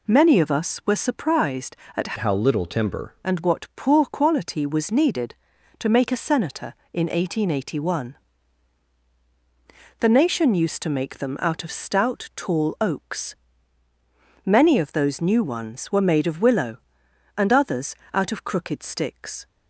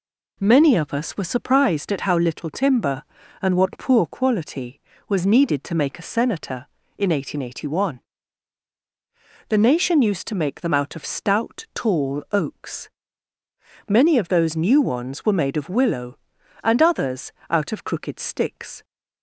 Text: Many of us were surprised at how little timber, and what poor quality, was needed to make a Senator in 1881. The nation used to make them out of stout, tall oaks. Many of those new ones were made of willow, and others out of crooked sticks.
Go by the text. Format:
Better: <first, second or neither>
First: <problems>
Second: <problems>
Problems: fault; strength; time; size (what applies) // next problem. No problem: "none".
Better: second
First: changes voice from "how" to "timber"; from 2.1 to 3.1 s; 1.0 s long // pauses between "others" and "out"; slight; at 17.9 s; 0.18 s long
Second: pauses between "others" and "out"; slight; at 17.3 s; 0.18 s long